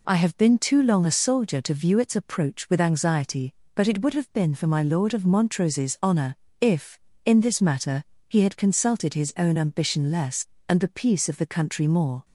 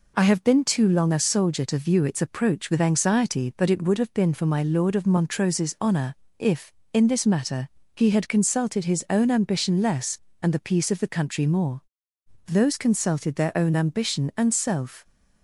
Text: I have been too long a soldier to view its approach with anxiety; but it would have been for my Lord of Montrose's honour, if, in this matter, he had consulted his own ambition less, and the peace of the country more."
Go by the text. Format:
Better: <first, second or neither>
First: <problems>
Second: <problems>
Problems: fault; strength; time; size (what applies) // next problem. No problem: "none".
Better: first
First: none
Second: goes on to say "Those consulted their own ambition and self"; strong; from 12.4 s on; 2.5 s long